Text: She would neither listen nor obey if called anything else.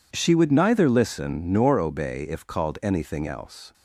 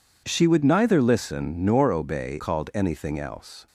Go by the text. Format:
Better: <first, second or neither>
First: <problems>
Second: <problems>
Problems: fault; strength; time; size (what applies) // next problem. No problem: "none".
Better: first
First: none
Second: skips "if"; at 2.3 s